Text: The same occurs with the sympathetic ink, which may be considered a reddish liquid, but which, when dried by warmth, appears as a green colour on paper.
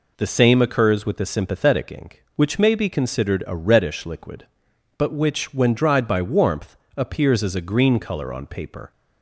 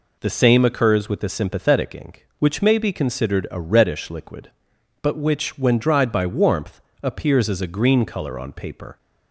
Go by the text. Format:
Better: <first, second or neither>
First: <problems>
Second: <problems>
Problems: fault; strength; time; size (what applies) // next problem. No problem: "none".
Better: neither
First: none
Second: none